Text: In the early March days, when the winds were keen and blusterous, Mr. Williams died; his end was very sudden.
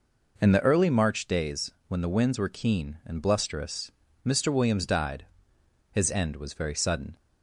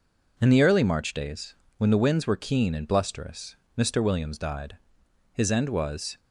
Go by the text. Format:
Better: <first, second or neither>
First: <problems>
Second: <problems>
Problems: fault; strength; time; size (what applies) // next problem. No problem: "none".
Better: first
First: none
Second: stops before "very sudden"; at 6.1 s